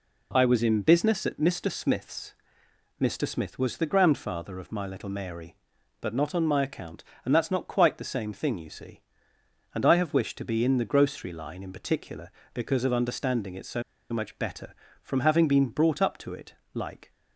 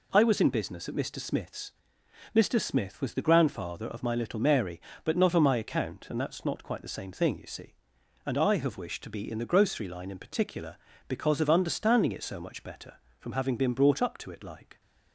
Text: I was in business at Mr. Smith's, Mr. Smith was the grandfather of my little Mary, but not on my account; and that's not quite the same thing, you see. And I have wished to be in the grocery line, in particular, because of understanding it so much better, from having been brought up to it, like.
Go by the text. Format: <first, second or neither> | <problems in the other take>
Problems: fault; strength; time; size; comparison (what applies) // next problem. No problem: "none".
second | pauses between "so" and "much"; slight; at 13.8 s; 0.28 s long